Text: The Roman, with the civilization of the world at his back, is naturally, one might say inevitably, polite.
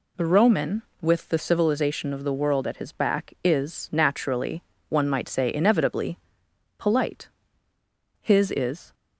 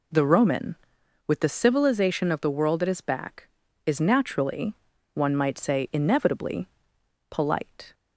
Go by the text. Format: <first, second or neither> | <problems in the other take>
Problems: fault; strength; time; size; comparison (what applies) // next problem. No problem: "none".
second | goes on to say "His is"; noticeable; from 8.2 s on; 0.72 s long